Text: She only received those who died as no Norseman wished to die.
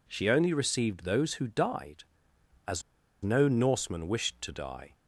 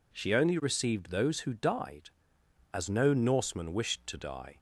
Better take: second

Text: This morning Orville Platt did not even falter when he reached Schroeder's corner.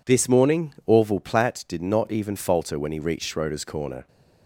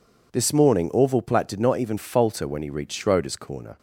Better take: neither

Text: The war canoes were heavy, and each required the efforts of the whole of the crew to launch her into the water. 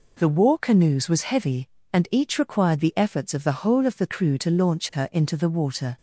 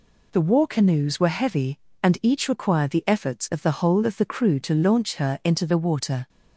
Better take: second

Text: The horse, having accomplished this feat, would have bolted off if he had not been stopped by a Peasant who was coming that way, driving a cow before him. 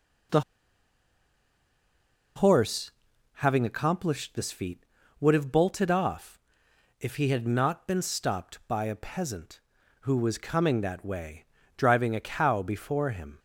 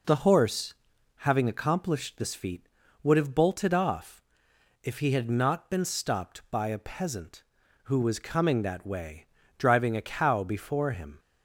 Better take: second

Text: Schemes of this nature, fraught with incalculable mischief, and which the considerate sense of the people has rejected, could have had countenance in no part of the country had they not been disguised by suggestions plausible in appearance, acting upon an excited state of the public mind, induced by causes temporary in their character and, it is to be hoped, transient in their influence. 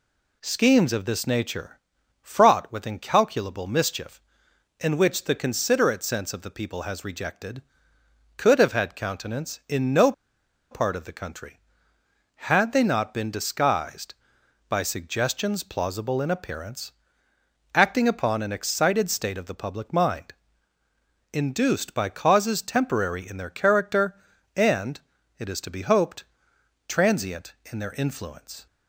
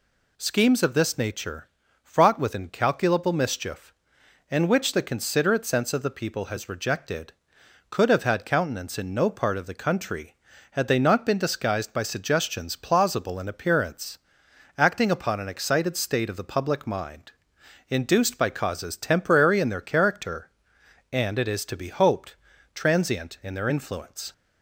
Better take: second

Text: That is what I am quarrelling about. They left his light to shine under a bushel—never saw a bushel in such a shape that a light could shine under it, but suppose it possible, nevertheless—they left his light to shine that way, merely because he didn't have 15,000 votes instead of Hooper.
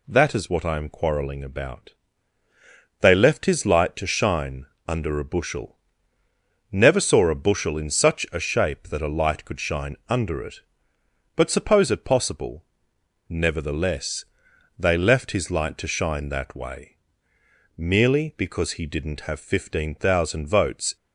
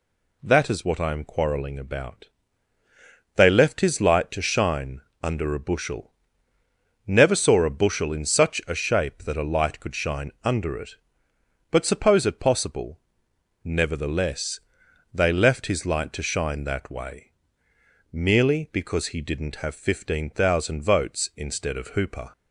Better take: second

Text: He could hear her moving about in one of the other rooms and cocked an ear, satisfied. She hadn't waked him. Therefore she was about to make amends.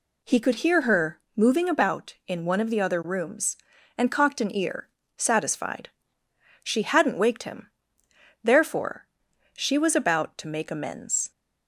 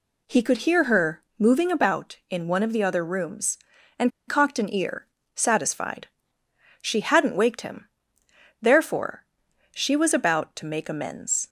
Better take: first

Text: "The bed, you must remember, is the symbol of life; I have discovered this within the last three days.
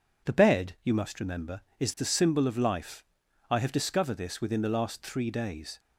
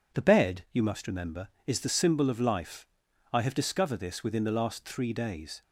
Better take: neither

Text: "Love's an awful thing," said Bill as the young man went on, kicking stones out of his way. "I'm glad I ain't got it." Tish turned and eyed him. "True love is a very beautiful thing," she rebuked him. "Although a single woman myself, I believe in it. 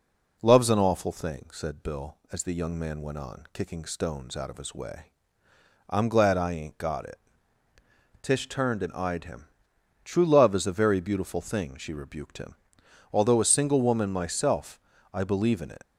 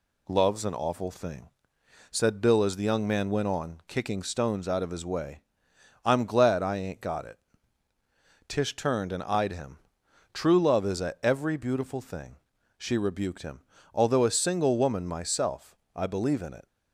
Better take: first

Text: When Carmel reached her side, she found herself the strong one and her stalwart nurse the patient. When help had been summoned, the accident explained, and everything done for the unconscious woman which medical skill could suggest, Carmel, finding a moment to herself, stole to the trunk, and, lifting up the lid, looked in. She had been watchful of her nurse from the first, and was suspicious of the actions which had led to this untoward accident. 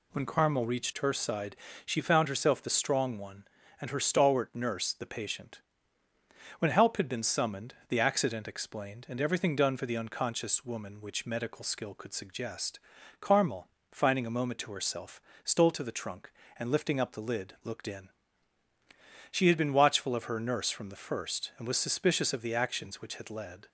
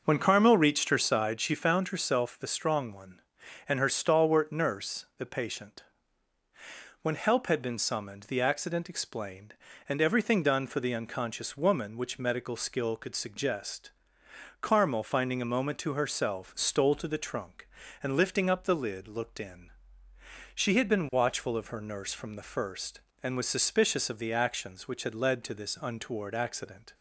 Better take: second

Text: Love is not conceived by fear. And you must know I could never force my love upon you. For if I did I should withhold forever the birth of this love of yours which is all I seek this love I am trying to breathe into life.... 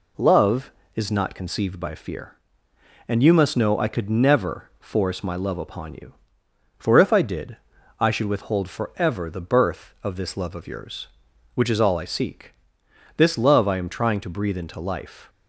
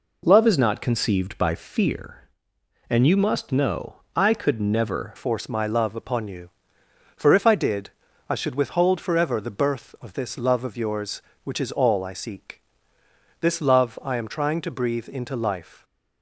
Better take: first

